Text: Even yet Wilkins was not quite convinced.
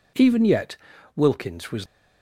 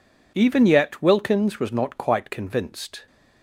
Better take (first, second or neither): second